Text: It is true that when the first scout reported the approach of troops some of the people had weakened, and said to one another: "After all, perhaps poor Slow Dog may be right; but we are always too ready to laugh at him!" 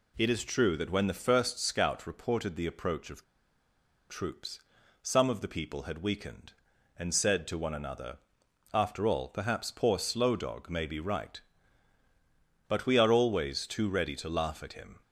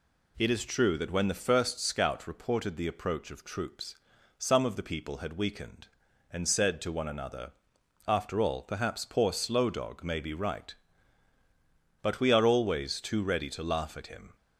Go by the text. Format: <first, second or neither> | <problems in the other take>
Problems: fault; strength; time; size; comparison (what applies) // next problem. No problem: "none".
second | pauses between "of" and "troops"; noticeable; at 3.2 s; 0.86 s long // pauses between "troops" and "some"; at 4.5 s; 0.42 s long; also in the second